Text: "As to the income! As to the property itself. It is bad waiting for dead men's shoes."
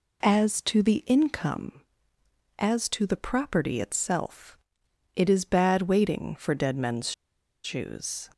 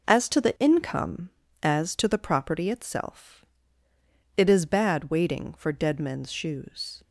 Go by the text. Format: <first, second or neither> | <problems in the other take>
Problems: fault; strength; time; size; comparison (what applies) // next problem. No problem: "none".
second | pauses between "men's" and "shoes"; noticeable; at 7.1 s; 0.52 s long